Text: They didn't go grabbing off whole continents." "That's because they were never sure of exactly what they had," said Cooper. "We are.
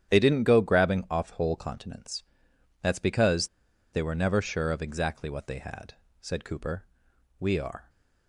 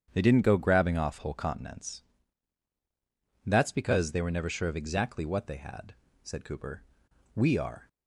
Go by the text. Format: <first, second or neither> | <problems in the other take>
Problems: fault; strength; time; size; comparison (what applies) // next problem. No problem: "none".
second | starts louder than the rest; strong; until 1.1 s; 9.5 dB; strong in the second // pauses between "because" and "they"; at 3.4 s; 0.44 s long